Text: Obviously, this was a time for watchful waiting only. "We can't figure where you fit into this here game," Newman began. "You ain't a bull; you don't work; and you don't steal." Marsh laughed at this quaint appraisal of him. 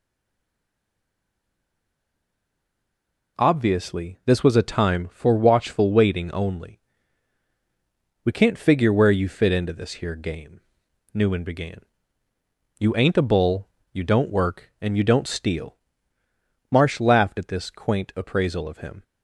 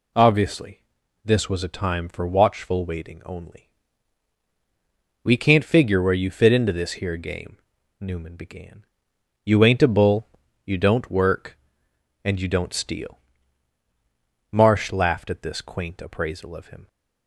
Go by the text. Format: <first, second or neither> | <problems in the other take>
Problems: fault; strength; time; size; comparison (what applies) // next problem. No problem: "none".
second | stays silent before the first word; strong; until 3.3 s; 3.3 s long